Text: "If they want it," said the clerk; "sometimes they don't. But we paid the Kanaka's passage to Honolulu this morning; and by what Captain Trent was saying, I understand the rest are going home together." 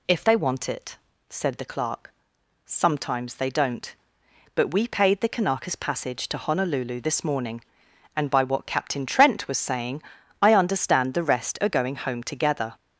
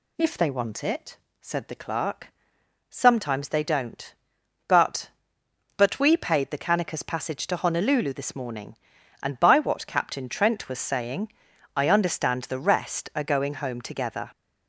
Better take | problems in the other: first | says "But" twice; at 5.7 s

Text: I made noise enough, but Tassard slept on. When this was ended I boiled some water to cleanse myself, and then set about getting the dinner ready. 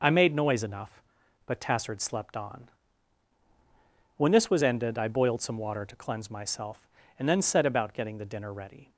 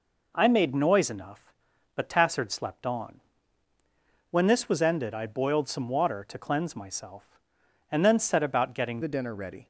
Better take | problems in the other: first | changes voice at "the"; from 9.0 s on; 0.6 s long

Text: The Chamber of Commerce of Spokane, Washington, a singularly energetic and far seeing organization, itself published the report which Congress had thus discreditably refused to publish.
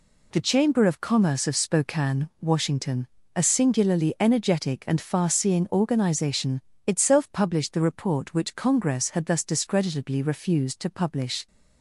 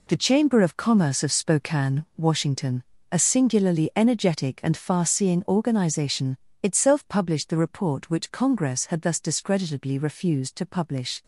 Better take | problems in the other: first | gets quieter; strong; throughout; 9.5 dB

